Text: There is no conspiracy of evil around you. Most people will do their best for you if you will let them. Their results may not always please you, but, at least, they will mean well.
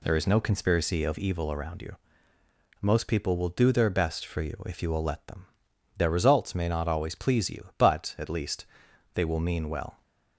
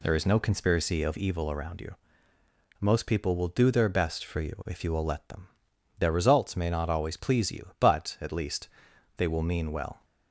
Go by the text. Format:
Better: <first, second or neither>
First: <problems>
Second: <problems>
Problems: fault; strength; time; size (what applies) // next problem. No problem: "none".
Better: neither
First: none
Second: none